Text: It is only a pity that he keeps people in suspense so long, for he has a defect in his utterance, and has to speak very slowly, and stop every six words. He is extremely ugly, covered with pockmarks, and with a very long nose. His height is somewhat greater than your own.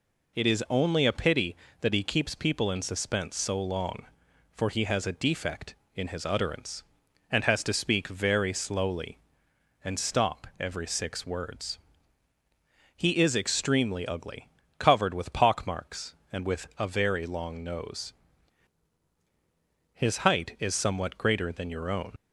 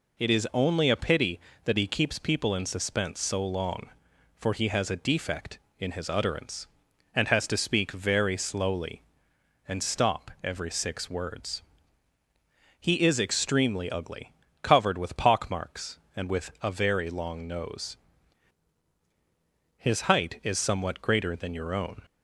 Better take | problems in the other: second | leaves "own" unfinished; at 22.1 s; 50 ms

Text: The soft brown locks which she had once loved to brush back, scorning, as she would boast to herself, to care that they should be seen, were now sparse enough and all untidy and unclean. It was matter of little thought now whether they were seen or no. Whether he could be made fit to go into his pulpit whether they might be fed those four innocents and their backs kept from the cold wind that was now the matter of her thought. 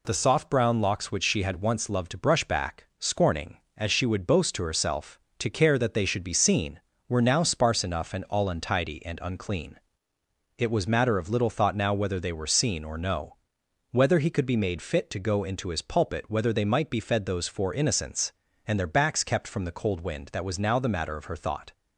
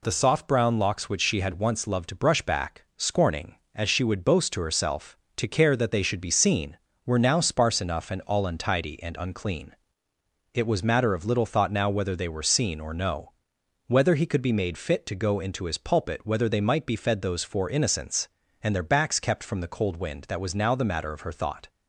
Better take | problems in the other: neither | none

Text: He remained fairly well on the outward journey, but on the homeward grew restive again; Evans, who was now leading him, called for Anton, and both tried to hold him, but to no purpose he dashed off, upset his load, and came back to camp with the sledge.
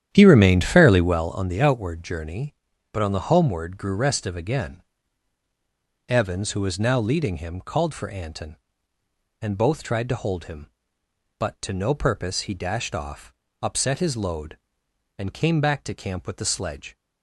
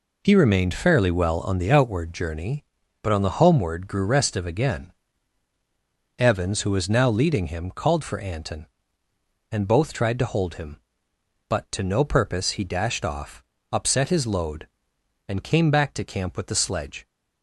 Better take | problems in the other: second | starts louder than the rest; strong; until 1.2 s; 10 dB

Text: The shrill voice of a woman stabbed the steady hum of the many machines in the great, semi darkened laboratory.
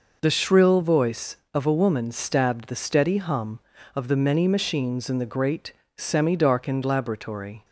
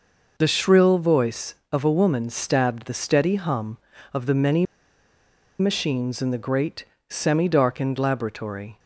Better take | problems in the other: first | pauses between "many" and "machines"; noticeable; at 4.6 s; 0.94 s long

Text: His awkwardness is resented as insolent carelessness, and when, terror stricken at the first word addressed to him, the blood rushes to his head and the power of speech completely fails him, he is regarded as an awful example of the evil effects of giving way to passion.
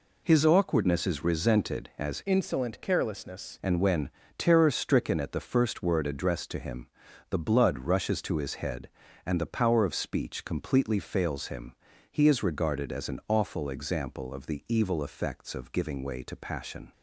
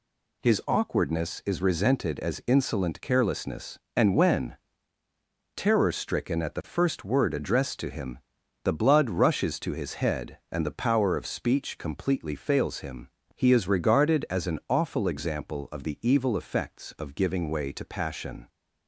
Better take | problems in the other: second | changes voice from "insolent" to "carelessness"; from 2.2 to 3.5 s; 1.3 s long

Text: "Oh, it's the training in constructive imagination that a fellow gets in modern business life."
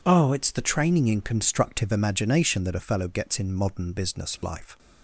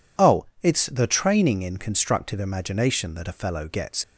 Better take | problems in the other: first | stops before "in modern business life"; at 4.0 s

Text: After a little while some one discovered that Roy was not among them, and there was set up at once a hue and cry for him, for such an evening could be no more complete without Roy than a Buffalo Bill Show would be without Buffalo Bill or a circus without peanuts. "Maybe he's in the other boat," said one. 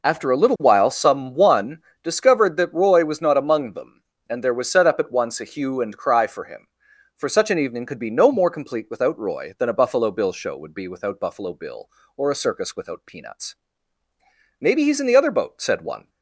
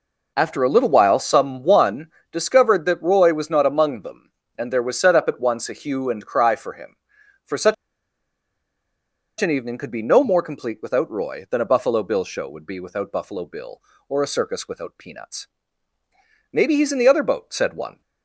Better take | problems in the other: first | pauses between "one" and "discovered"; slight; at 2.0 s; 0.22 s long; slight in the first // pauses between "such" and "an"; strong; at 7.7 s; 1.6 s long

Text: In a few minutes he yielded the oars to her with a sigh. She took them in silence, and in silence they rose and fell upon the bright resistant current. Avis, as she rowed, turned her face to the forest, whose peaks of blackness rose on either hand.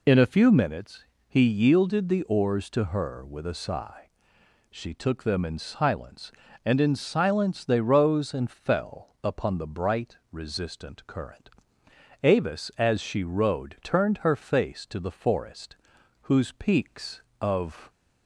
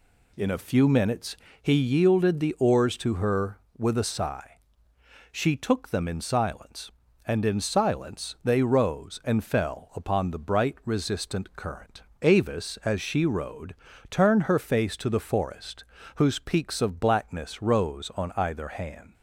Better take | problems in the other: second | pauses between "minutes" and "he"; slight; at 1.0 s; 0.24 s long; slight in the second // stops before "blackness rose on either hand"; at 17.8 s

